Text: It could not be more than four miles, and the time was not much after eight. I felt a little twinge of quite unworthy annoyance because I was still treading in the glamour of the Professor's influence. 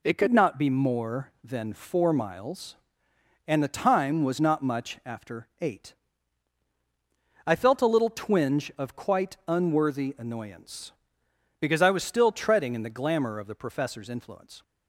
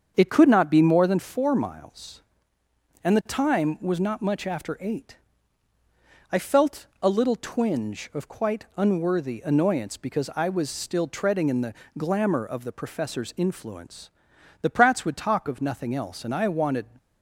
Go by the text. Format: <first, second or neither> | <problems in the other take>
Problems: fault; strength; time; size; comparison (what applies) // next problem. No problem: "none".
first | starts louder than the rest; until 1.1 s; 7 dB // pauses between "felt" and "a"; slight; at 6.8 s; 0.16 s long // pauses between "the" and "glamour"; slight; at 11.7 s; 0.24 s long // goes on to say "The Pratts would talk of nothing else and I wanted"; strong; from 14.5 s on; 2.2 s long